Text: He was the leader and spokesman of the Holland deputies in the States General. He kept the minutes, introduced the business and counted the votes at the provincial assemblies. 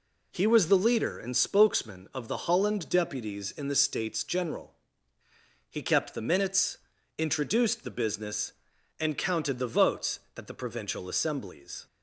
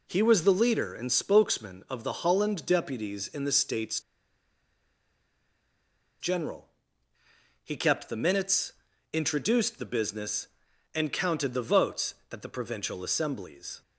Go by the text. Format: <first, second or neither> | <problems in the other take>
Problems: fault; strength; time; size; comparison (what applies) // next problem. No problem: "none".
first | pauses between "States" and "General"; strong; at 3.9 s; 2.2 s long